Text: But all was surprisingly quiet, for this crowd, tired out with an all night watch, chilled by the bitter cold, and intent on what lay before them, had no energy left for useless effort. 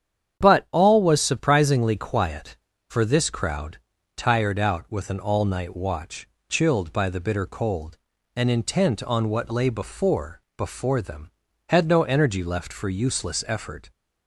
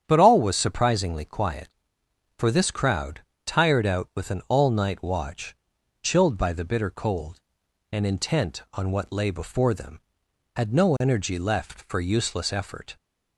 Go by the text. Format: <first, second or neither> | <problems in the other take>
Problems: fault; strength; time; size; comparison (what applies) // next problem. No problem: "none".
second | starts louder than the rest; strong; until 1.4 s; 8.5 dB; strong in the second // says "before" twice; at 10.5 s